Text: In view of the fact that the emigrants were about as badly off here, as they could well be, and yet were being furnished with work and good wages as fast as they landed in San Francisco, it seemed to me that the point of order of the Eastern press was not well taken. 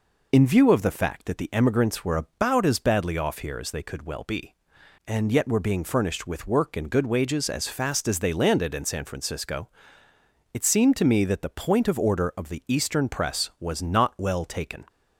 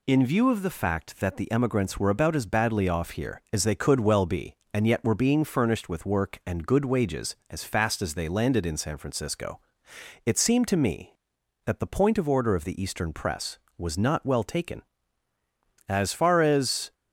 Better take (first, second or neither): first